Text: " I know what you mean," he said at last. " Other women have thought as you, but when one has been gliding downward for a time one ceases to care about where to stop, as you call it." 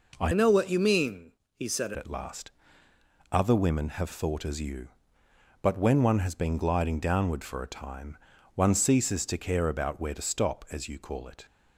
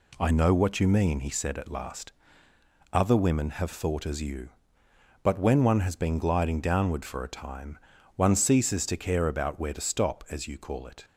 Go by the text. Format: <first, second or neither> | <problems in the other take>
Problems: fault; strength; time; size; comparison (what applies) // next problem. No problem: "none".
second | changes voice from "know" to "said"; from 0.3 to 1.9 s; 1.6 s long // pauses between "time" and "one"; at 8.1 s; 0.38 s long; also in the second